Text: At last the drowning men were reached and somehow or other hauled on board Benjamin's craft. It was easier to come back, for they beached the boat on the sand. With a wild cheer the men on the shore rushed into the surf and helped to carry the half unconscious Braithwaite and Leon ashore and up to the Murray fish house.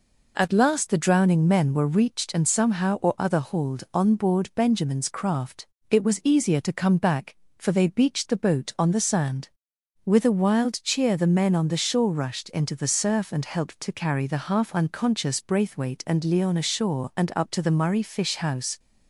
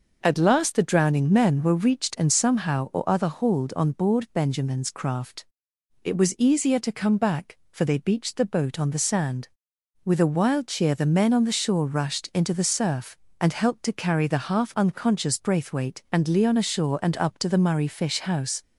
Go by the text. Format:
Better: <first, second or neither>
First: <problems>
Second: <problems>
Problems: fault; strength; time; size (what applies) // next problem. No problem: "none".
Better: neither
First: none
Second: none